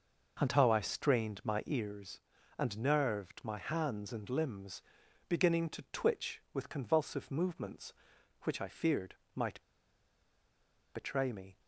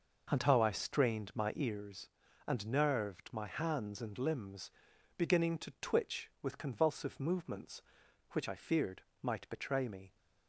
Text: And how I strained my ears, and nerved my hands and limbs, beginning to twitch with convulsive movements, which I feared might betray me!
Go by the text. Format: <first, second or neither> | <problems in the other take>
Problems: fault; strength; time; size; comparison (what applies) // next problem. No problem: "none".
second | pauses between "feared" and "might"; slight; at 9.1 s; 0.18 s long; slight in the second // pauses between "might" and "betray"; strong; at 9.5 s; 1.3 s long